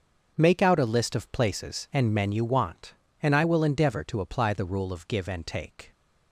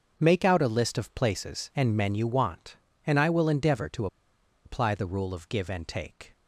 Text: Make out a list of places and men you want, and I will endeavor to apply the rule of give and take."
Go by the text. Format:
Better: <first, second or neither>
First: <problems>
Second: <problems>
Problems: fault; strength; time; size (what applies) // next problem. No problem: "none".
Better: first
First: starts louder than the rest; until 1.3 s; 6.5 dB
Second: starts louder than the rest; until 1.1 s; 6.5 dB // pauses between "to" and "apply"; noticeable; at 4.0 s; 0.59 s long